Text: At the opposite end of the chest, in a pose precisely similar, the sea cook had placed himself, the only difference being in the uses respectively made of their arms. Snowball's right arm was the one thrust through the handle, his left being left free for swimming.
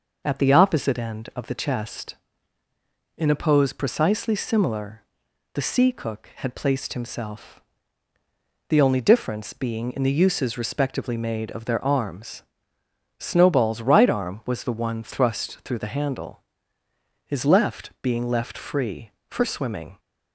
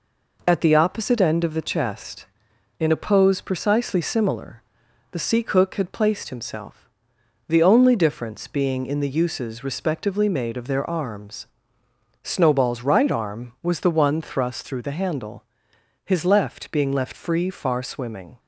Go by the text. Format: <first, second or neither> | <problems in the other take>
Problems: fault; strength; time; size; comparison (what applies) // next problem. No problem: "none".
first | says "far" for "for"; at 17.5 s